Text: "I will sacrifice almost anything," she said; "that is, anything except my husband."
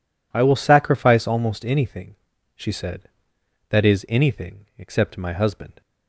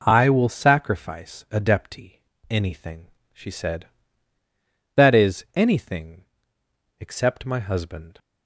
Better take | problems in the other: first | says "adepti" for "almost"; at 1.5 s // pauses between "anything" and "except"; noticeable; at 6.2 s; 0.74 s long

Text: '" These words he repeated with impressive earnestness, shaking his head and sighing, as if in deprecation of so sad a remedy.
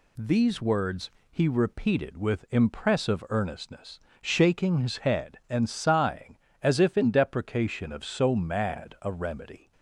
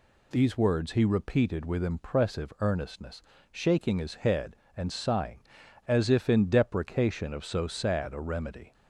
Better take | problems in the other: second | pauses between "words" and "he"; slight; at 1.1 s; 0.20 s long // says "mad" for "sad"; at 8.3 s

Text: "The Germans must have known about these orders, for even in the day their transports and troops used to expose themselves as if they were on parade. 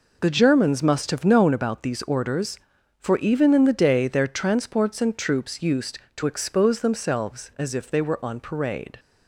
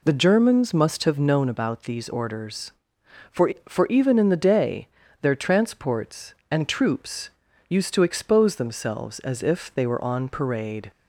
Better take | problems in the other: first | says "for" twice; at 3.6 s // pauses between "day" and "their"; slight; at 4.8 s; 0.32 s long // pauses between "troops" and "used"; at 7.3 s; 0.38 s long

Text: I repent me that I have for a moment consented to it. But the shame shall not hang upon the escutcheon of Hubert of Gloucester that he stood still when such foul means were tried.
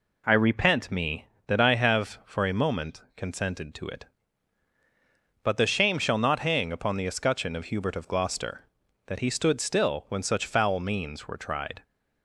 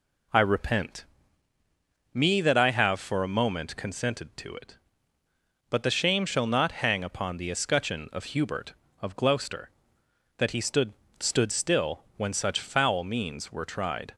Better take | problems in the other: first | pauses between "repent" and "me"; at 1.0 s; 1.0 s long // says "stood" twice; at 11.1 s

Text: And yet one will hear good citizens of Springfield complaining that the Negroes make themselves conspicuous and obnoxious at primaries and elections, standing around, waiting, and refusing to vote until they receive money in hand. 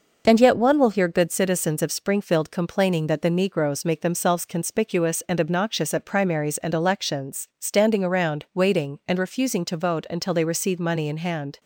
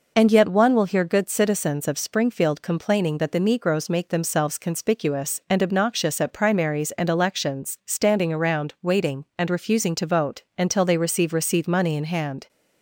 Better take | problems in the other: first | pauses between "vote" and "until"; slight; at 10.4 s; 0.16 s long // says "receive" twice; at 11.3 s

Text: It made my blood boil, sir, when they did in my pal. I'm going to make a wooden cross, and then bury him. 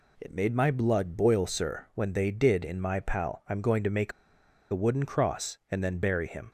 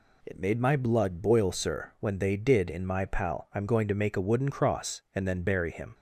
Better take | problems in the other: second | pauses between "make" and "a"; noticeable; at 4.1 s; 0.60 s long

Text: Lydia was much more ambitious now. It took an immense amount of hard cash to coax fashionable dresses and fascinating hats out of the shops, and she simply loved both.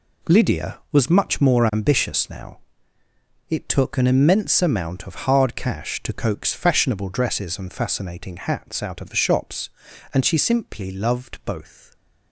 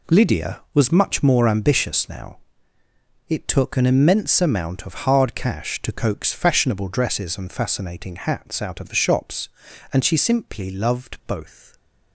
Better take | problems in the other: neither | none

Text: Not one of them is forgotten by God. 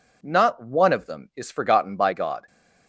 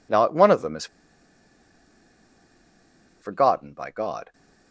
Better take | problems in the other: first | pauses between "is" and "forgotten"; strong; at 0.8 s; 2.3 s long

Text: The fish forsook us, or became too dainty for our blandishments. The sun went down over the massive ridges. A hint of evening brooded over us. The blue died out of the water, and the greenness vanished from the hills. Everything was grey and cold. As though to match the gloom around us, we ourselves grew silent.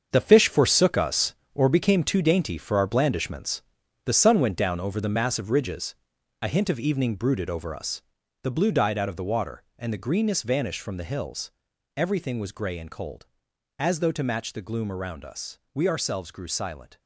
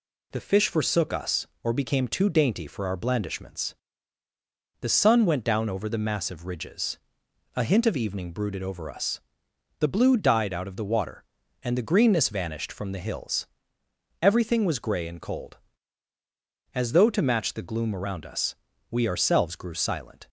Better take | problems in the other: second | gets quieter; strong; throughout; 10 dB

